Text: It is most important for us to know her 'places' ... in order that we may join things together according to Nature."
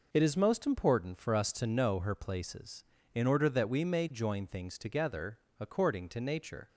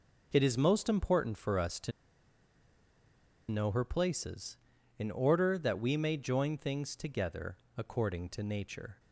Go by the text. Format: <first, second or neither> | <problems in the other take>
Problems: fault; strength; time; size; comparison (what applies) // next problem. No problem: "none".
first | pauses between "to" and "know"; strong; at 1.9 s; 1.5 s long // pauses between "together" and "according"; slight; at 7.5 s; 0.20 s long; slight in the first